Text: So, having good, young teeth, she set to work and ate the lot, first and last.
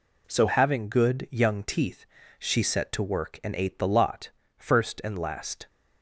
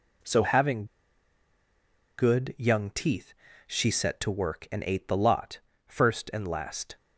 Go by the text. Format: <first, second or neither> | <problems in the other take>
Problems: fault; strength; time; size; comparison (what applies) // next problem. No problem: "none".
first | pauses between "having" and "good"; strong; at 0.8 s; 1.3 s long